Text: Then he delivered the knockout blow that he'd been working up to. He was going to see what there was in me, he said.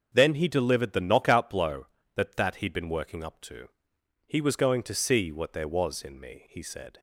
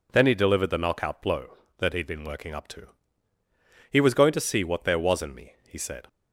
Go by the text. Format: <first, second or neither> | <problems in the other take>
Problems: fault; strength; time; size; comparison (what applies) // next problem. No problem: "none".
second | starts louder than the rest; until 1.1 s; 6.5 dB // says "that" twice; at 2.3 s